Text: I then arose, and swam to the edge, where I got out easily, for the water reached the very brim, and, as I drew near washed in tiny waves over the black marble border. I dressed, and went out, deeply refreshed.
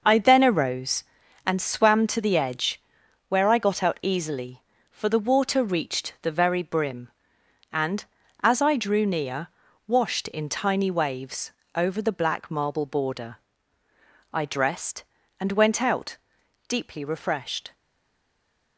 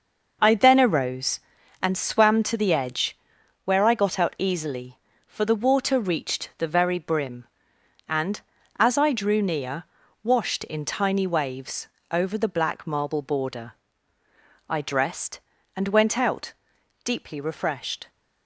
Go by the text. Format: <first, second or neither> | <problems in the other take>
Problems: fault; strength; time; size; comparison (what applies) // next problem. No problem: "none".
second | pauses between "near" and "washed"; at 9.4 s; 0.38 s long; also in the second // pauses between "waves" and "over"; slight; at 11.5 s; 0.24 s long; slight in the second // stays silent after the last word; from 17.7 s on; 1.0 s long